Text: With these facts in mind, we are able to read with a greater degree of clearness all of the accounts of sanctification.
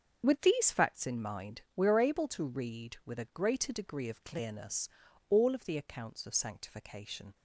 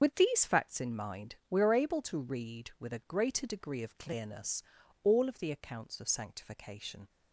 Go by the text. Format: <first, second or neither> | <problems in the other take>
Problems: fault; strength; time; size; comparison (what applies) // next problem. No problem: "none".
first | loses the start of "With"; at 0.0 s; 35 ms // starts louder than the rest; until 1.0 s; 7 dB; also in the first // pauses between "clearness" and "all"; at 4.6 s; 0.40 s long; also in the first